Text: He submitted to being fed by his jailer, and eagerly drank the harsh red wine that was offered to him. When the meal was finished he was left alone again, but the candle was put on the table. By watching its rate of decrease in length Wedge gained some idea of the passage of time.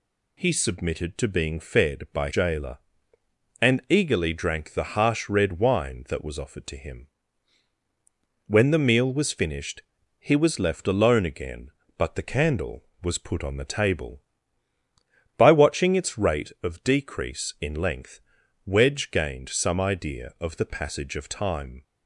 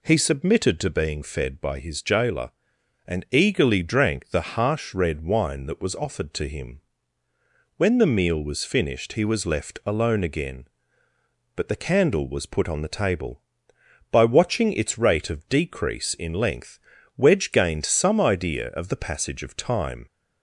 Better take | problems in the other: second | skips "his"; at 2.3 s // pauses between "finished" and "he"; slight; at 9.8 s; 0.36 s long // pauses between "length" and "Wedge"; at 18.2 s; 0.44 s long; also in the second

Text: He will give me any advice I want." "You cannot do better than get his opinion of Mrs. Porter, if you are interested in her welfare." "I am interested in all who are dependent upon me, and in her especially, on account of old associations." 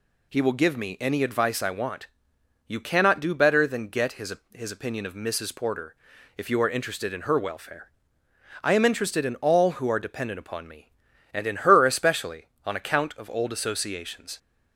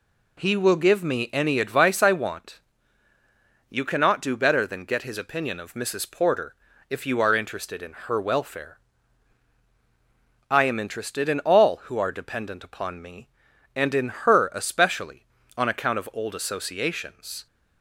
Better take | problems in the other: second | says "his" twice; at 4.5 s

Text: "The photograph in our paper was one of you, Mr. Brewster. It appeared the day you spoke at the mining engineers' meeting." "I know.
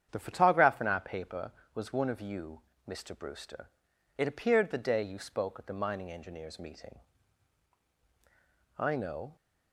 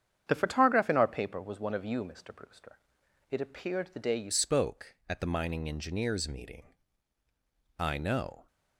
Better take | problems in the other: first | starts louder than the rest; strong; until 1.2 s; 8.5 dB; strong in the first // changes voice at "spoke"; from 4.3 s on; 4.1 s long

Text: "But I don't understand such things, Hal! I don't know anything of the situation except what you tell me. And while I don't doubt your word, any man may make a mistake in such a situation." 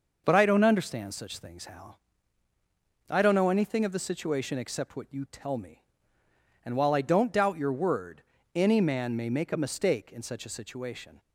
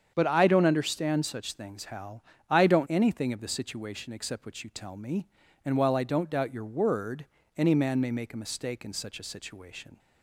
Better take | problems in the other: first | starts louder than the rest; strong; until 1.1 s; 7.5 dB // skips "know"; at 2.8 s

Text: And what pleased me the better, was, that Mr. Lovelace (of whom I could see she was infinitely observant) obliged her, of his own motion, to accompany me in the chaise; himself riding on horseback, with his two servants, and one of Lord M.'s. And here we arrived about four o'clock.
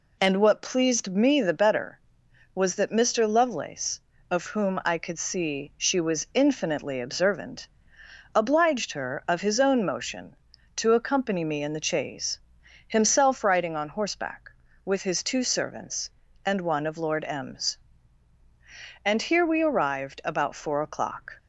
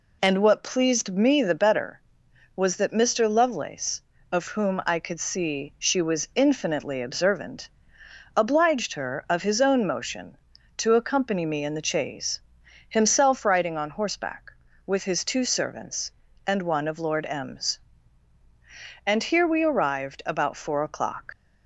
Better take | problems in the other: first | leaves "o'clock" unfinished; at 21.3 s; 65 ms

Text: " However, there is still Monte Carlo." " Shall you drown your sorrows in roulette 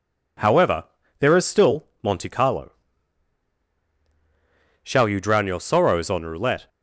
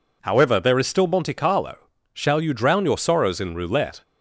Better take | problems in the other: second | says "on" for "in"; at 6.1 s

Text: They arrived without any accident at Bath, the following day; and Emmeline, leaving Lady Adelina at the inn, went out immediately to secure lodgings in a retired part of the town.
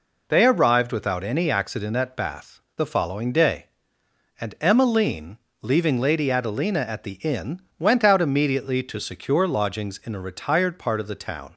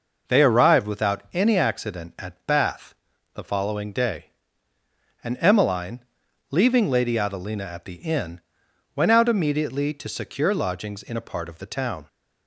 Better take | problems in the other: first | skips "retired"; at 11.2 s

